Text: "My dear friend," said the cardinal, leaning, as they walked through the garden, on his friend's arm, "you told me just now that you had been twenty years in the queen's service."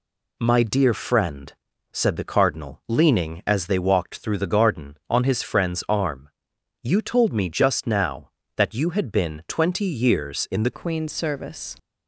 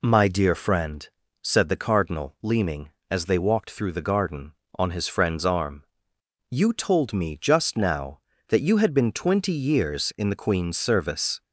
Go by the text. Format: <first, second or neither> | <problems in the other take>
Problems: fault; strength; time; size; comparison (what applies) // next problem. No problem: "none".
second | changes voice at "queen's"; from 10.7 s on; 1.0 s long